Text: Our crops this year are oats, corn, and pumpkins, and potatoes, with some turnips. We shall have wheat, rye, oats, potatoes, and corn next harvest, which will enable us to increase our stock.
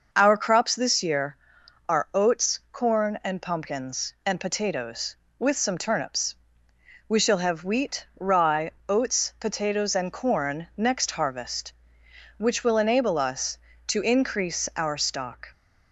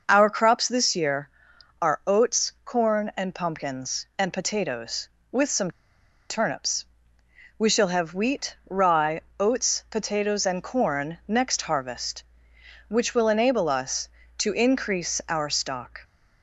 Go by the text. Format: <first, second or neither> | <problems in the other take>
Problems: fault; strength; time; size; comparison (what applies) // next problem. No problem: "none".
first | pauses between "some" and "turnips"; noticeable; at 5.6 s; 0.59 s long